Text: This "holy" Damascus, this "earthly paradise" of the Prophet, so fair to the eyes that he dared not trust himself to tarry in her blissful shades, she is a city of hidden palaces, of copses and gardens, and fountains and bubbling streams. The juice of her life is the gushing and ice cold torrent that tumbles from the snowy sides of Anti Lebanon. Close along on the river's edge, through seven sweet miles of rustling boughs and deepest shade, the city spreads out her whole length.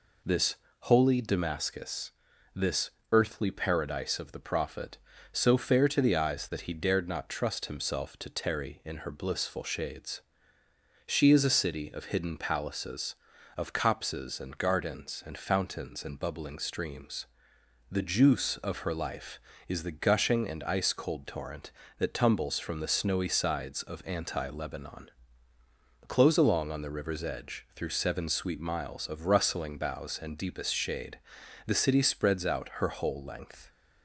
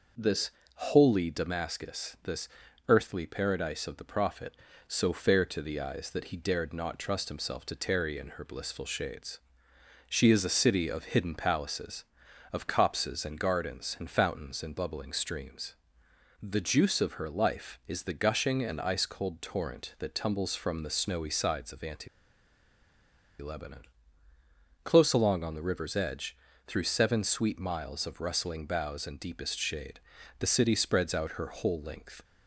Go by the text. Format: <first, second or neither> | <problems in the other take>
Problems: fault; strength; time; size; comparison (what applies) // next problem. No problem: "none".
first | pauses between "This" and "holy"; slight; at 0.5 s; 0.26 s long; slight in the first // pauses between "this" and "earthly"; at 2.4 s; 0.40 s long; slight in the first // pauses between "Anti" and "Lebanon"; strong; at 22.0 s; 1.3 s long